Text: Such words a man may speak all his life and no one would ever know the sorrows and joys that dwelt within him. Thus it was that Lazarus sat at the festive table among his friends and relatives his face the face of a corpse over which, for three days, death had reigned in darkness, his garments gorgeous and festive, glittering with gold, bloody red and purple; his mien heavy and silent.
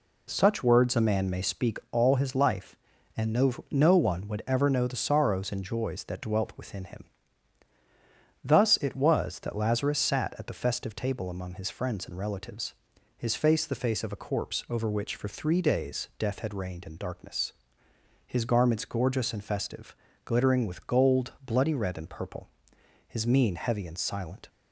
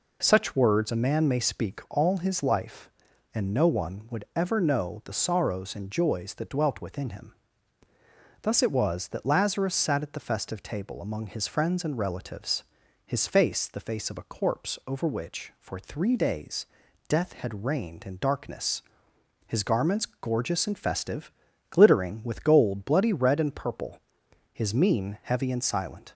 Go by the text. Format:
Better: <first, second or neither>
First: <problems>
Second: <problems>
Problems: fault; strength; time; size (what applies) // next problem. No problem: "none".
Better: second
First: says "no" twice; at 3.7 s // pauses between "relatives" and "his"; at 12.7 s; 0.42 s long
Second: pauses between "relatives" and "his"; at 12.6 s; 0.42 s long